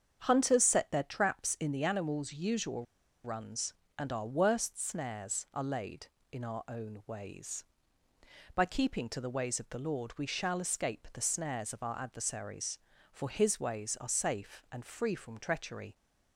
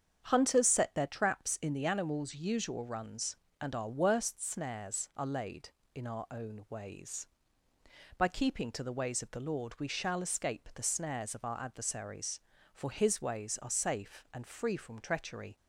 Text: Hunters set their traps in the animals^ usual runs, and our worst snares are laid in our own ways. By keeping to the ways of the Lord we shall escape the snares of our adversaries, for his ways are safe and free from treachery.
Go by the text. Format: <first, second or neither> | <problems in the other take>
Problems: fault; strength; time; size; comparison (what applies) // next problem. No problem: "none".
second | starts louder than the rest; strong; until 1.2 s; 7.5 dB; strong in the second // pauses between "usual" and "runs"; at 2.8 s; 0.40 s long